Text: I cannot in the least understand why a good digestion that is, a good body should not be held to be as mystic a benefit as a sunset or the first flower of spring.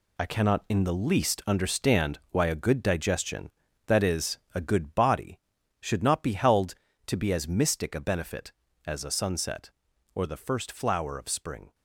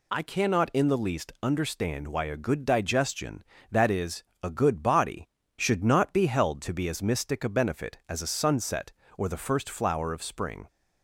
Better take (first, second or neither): second